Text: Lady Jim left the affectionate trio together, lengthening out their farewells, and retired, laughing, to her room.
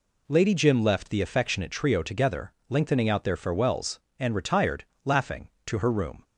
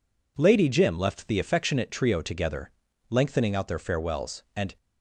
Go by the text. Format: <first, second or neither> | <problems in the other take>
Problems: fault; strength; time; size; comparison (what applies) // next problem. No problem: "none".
first | stops before "retired laughing to her room"; at 4.7 s